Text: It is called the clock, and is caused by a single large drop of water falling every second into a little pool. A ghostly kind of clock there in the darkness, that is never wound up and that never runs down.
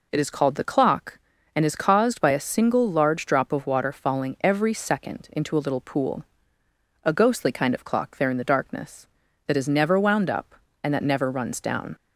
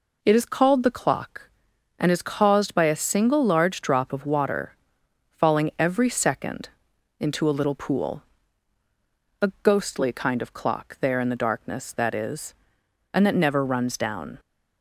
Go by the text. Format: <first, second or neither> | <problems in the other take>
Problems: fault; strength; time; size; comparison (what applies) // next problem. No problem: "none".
first | pauses between "water" and "falling"; noticeable; at 4.7 s; 0.58 s long // pauses between "second" and "into"; noticeable; at 6.6 s; 0.50 s long // skips "never wound up"; at 12.8 s